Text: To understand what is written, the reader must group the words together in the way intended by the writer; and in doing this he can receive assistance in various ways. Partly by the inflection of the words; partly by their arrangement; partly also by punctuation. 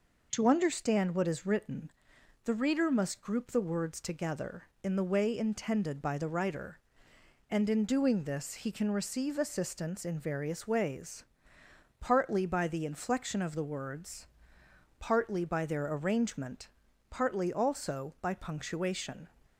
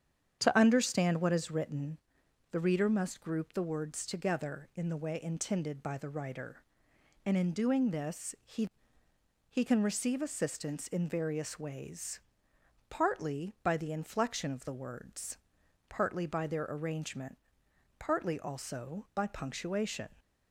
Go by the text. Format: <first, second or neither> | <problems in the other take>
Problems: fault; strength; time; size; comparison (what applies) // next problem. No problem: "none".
first | starts louder than the rest; strong; until 1.4 s; 8.5 dB // says "he" twice; at 9.4 s